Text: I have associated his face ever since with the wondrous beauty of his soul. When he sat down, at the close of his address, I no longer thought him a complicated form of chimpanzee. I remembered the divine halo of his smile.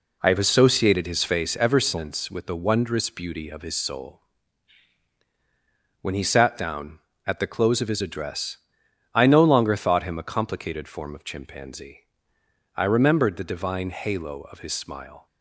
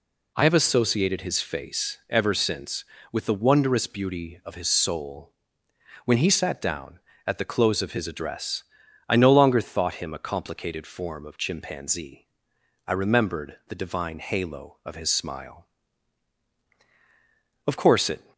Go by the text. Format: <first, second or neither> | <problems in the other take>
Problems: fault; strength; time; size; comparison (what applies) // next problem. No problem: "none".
first | goes on to say "Of course it"; noticeable; from 17.6 s on; 0.64 s long